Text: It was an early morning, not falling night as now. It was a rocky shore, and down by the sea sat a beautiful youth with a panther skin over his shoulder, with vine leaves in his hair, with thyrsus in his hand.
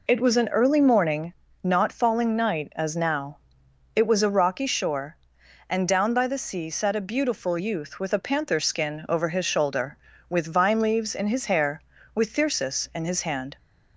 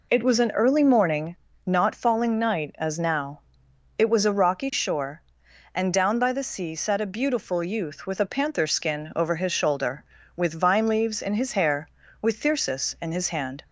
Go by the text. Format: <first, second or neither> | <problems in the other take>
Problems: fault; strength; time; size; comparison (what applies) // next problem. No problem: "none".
neither | none